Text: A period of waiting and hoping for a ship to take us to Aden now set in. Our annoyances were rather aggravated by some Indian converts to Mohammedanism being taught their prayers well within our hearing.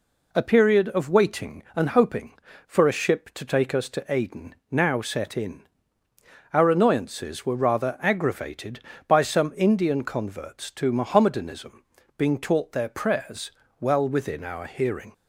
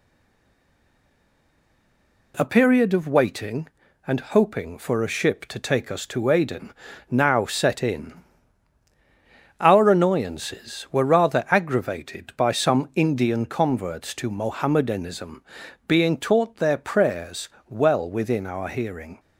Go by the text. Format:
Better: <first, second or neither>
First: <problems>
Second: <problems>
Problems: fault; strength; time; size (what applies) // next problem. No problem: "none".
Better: first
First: pauses between "Aden" and "now"; slight; at 4.5 s; 0.16 s long // pauses between "Mohammedanism" and "being"; slight; at 11.8 s; 0.34 s long // pauses between "prayers" and "well"; slight; at 13.5 s; 0.30 s long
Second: stays silent before the first word; until 2.3 s; 2.3 s long // pauses between "Aden" and "now"; slight; at 6.7 s; 0.36 s long // pauses between "Mohammedanism" and "being"; at 15.4 s; 0.44 s long // pauses between "prayers" and "well"; slight; at 17.4 s; 0.22 s long